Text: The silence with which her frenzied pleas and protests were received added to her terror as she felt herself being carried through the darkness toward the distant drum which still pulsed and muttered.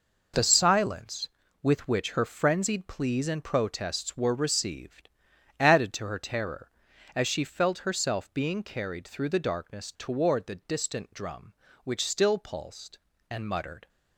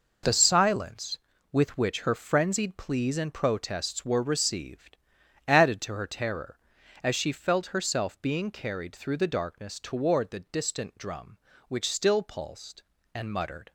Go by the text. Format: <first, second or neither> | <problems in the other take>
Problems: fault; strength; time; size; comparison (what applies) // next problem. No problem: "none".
neither | pauses between "received" and "added"; noticeable; the same in both